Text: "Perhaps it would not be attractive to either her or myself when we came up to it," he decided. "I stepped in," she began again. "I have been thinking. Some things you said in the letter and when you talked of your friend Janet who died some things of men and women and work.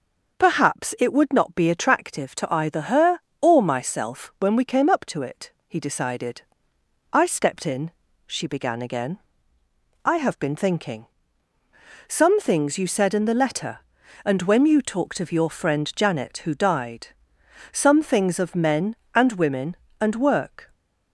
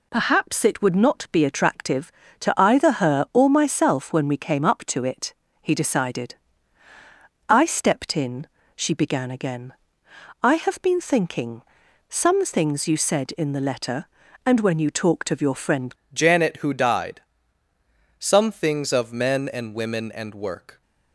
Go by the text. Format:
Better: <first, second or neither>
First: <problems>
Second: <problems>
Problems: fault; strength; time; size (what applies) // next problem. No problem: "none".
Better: first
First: pauses between "died" and "some"; noticeable; at 17.0 s; 0.62 s long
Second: changes voice at "Janet"; from 16.1 s on; 4.7 s long // pauses between "died" and "some"; noticeable; at 17.2 s; 0.98 s long